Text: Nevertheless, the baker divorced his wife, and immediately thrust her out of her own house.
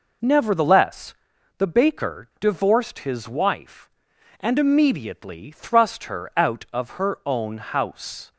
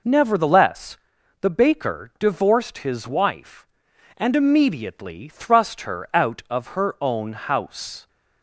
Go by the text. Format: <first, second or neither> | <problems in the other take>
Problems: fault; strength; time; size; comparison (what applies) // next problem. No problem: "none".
neither | none